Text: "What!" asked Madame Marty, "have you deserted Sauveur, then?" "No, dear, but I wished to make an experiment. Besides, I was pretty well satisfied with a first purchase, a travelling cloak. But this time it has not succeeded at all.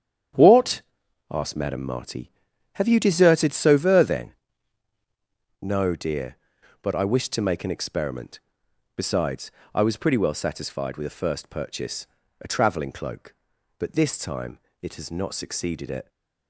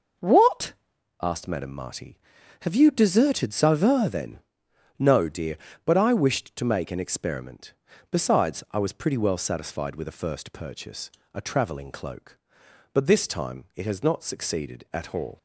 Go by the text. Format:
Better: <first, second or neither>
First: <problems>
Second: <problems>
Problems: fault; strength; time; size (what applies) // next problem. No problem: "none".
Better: second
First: starts louder than the rest; strong; until 1.8 s; 9 dB // pauses between "time" and "it"; slight; at 14.5 s; 0.24 s long // stops before "all"; at 16.0 s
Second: none